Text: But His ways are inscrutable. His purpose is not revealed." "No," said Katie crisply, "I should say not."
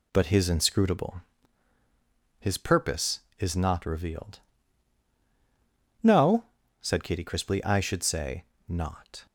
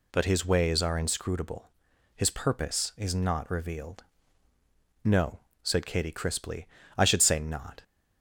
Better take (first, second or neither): second